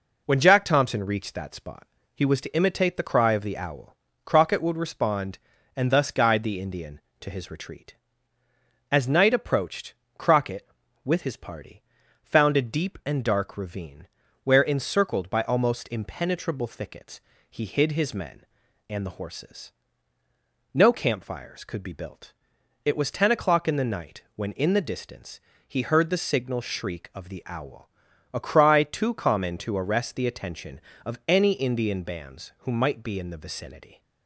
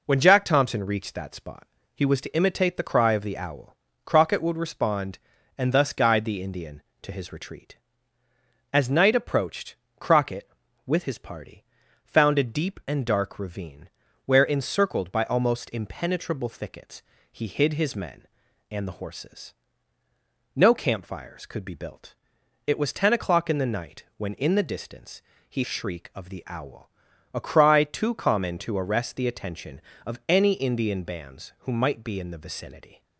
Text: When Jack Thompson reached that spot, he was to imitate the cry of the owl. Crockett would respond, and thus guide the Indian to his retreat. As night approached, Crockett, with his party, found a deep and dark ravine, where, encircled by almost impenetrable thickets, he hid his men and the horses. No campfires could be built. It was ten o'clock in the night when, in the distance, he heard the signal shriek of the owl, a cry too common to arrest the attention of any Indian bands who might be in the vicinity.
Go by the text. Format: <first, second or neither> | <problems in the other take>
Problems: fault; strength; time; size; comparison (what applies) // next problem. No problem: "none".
first | skips "heard the signal"; at 25.6 s